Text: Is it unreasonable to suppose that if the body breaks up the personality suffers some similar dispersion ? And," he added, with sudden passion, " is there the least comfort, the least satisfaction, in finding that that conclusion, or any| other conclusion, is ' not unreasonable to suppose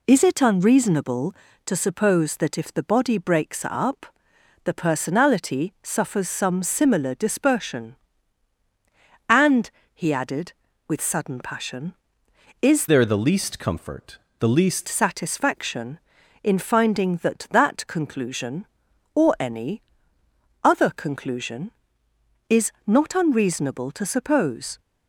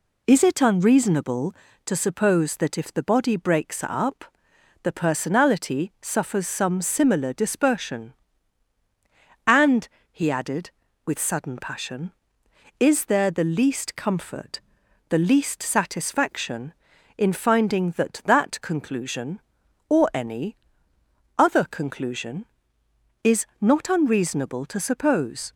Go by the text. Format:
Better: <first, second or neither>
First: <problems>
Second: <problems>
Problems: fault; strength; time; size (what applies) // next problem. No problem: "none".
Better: second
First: pauses between "up" and "the"; noticeable; at 4.0 s; 0.56 s long // changes voice from "there" to "least"; from 12.8 to 14.8 s; 2.0 s long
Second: pauses between "up" and "the"; noticeable; at 4.2 s; 0.56 s long